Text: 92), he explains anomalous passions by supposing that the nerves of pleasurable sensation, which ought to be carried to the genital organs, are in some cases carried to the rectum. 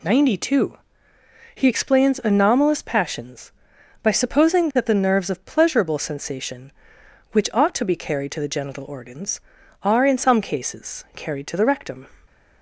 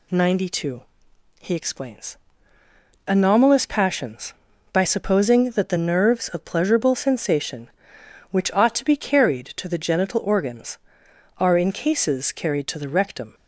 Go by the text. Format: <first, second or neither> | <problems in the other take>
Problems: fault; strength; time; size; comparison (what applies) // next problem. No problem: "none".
first | pauses between "explains" and "anomalous"; noticeable; at 2.1 s; 0.92 s long // skips "some"; at 11.7 s